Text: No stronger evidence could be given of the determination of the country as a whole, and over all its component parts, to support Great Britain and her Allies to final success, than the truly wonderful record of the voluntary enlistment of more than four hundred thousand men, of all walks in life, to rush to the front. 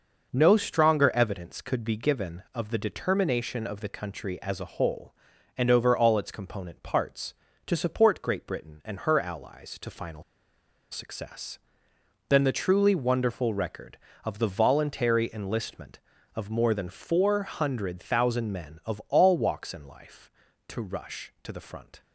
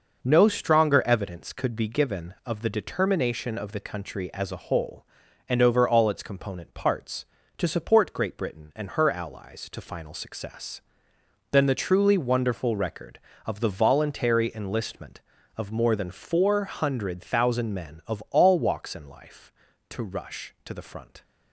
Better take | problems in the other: second | pauses between "final" and "success"; noticeable; at 10.2 s; 0.70 s long

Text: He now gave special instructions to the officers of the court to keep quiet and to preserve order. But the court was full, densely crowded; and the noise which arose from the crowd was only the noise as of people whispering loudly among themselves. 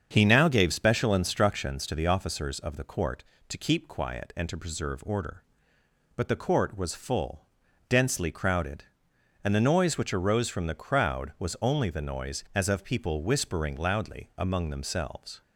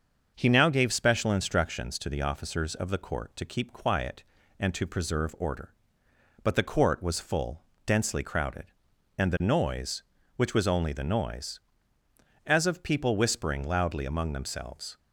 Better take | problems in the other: first | starts louder than the rest; until 1.3 s; 6.5 dB; strong in the first // skips "arose from the crowd"; at 10.5 s

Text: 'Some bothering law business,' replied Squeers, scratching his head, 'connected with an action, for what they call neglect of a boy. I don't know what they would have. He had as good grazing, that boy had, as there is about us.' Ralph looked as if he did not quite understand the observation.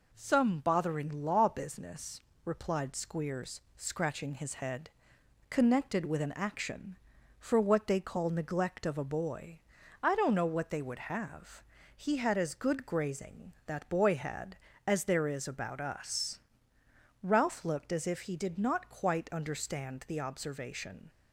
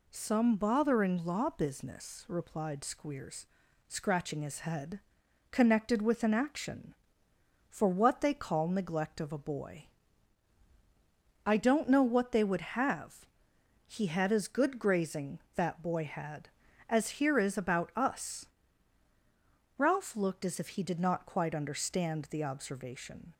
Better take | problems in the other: first | says "here" for "there"; at 17.2 s

